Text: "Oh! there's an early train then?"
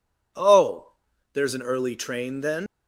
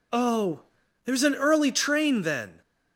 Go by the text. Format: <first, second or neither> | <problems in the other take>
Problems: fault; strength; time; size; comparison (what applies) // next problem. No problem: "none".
second | leaves "then" unfinished; at 2.6 s; 150 ms